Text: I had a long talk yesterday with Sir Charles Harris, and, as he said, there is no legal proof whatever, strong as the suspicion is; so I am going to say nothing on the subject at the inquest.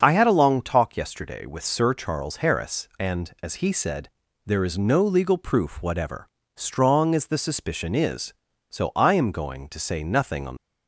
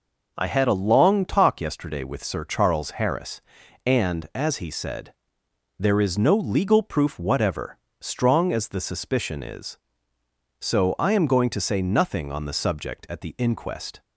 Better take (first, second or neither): second